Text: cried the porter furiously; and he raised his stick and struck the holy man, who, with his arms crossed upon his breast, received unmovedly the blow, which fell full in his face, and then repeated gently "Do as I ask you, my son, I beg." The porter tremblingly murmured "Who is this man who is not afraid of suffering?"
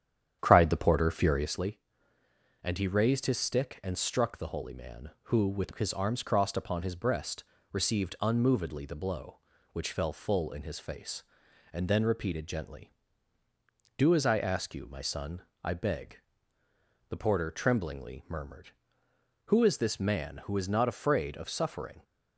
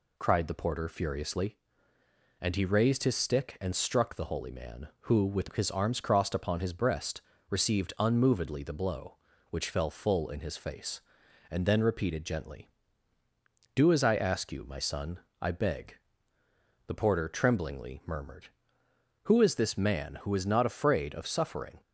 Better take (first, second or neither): second